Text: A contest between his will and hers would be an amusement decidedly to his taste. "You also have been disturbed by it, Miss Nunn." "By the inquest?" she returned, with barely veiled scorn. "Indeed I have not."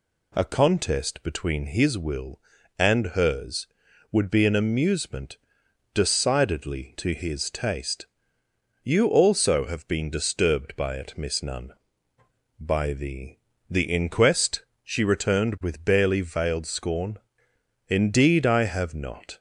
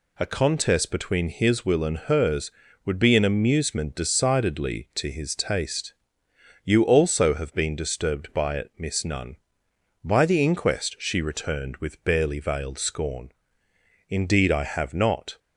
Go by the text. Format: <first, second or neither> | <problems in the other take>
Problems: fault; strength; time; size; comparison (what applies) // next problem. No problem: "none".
second | pauses between "amusement" and "decidedly"; noticeable; at 5.3 s; 0.56 s long // says "the" twice; at 13.6 s